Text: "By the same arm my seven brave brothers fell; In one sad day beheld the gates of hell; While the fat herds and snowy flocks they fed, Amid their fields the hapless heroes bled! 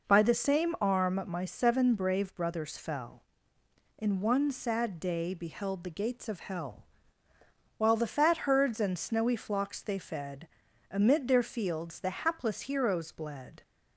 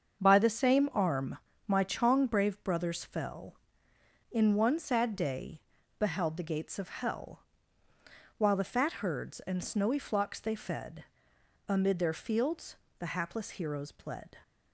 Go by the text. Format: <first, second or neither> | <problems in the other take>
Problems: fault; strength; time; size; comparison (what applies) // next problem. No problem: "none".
first | starts louder than the rest; until 1.2 s; 7 dB // pauses between "arm" and "my"; slight; at 1.3 s; 0.30 s long // says "chong" for "seven"; at 1.8 s // pauses between "day" and "beheld"; at 5.6 s; 0.38 s long // pauses between "fields" and "the"; slight; at 12.7 s; 0.22 s long